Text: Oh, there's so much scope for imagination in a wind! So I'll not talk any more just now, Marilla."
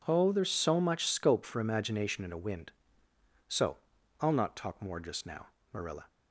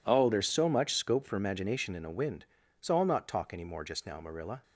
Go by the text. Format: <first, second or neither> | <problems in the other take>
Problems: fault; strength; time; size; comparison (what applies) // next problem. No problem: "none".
second | pauses between "So" and "I'll"; at 3.7 s; 0.42 s long // skips "any"; at 4.8 s